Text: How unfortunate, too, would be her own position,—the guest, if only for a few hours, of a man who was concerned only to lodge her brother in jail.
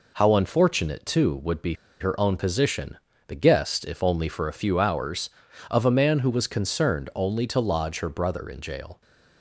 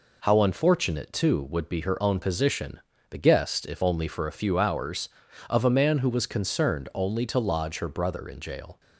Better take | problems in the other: second | pauses between "be" and "her"; slight; at 1.7 s; 0.25 s long

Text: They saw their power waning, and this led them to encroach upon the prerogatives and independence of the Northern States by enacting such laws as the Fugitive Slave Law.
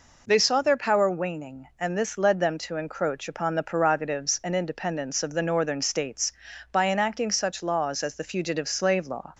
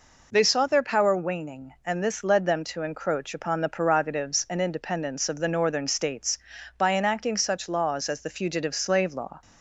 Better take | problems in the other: neither | none

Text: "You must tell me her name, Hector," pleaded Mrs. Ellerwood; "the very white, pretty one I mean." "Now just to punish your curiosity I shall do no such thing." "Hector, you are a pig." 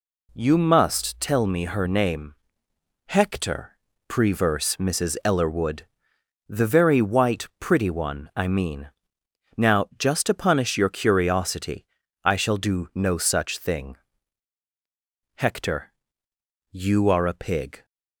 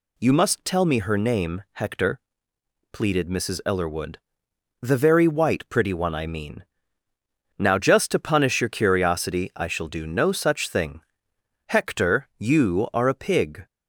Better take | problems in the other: second | says "preverse" for "pleaded"; at 4.0 s // pauses between "curiosity" and "I"; at 11.8 s; 0.40 s long

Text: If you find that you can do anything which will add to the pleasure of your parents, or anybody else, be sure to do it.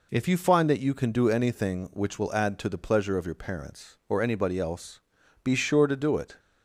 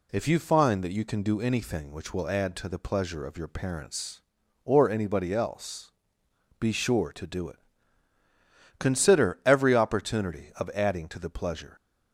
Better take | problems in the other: first | goes on to say "Consider every opportunity of adding to the pleasure"; strong; from 8.7 s on; 2.9 s long

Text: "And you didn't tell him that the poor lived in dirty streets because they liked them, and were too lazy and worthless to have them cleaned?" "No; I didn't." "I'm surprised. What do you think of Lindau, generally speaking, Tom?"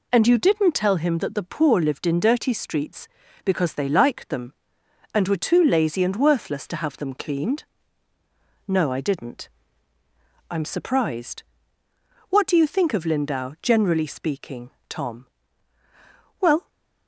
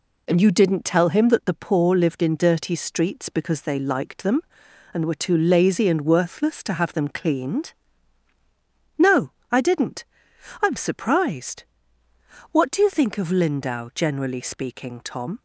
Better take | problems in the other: second | goes on to say "Well"; slight; from 16.3 s on; 0.28 s long

